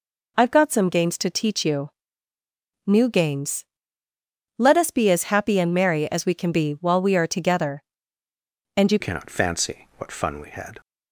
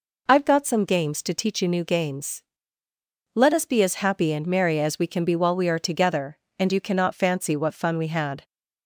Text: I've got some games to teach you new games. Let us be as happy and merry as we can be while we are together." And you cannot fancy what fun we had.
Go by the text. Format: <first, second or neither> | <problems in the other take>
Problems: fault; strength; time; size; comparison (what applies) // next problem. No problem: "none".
second | pauses between "you" and "new"; noticeable; at 1.9 s; 0.98 s long // changes voice at "cannot"; from 9.0 s on; 1.7 s long